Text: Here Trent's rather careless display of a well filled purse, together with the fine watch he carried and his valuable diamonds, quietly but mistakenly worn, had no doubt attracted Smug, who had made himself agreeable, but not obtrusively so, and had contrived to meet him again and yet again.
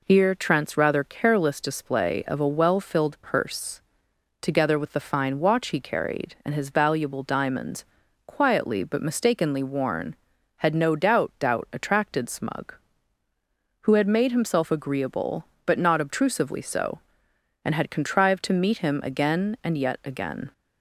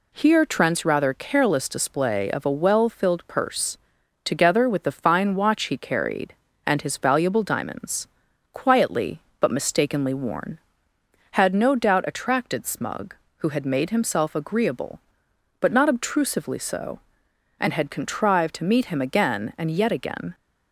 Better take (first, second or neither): second